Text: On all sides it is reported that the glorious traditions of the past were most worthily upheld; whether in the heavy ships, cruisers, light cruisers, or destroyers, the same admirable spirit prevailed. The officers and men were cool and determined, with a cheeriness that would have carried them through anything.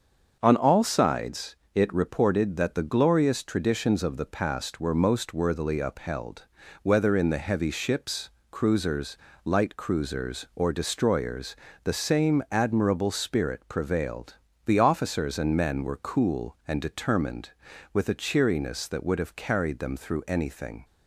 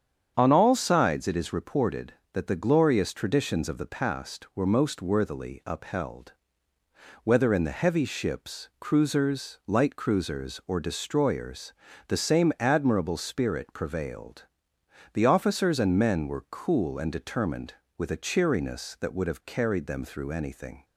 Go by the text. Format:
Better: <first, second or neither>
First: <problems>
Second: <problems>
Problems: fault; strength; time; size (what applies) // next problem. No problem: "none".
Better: second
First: starts louder than the rest; until 1.4 s; 7 dB // pauses between "sides" and "it"; slight; at 1.5 s; 0.18 s long // skips "is"; at 1.9 s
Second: starts louder than the rest; strong; until 1.3 s; 8 dB